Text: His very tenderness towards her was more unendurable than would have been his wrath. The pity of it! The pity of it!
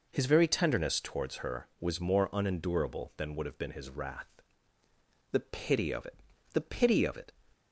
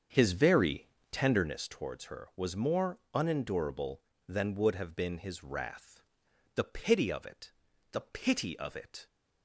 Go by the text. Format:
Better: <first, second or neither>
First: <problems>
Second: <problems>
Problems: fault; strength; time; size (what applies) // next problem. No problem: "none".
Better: first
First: none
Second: starts louder than the rest; until 1.5 s; 7 dB // pauses between "very" and "tenderness"; slight; at 0.8 s; 0.24 s long // pauses between "more" and "unendurable"; slight; at 2.9 s; 0.16 s long